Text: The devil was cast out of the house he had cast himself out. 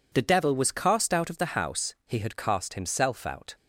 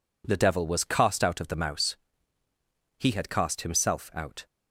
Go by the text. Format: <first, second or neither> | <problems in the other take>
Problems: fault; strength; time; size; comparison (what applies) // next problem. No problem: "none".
first | says "mouse" for "house"; at 1.5 s